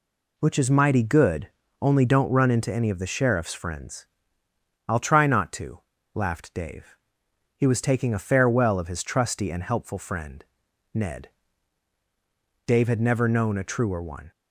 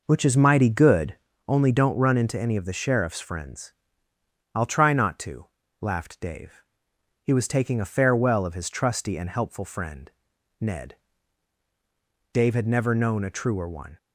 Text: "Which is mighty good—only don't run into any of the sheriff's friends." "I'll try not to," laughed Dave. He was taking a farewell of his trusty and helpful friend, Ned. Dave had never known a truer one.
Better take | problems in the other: first | starts louder than the rest; noticeable; until 1.3 s; 5 dB

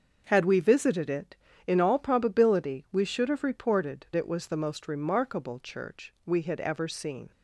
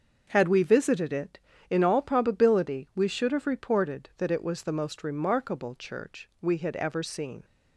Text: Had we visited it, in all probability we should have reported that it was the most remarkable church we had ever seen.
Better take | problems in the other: second | starts louder than the rest; until 1.2 s; 6.5 dB; also in the second // skips "that"; at 4.1 s

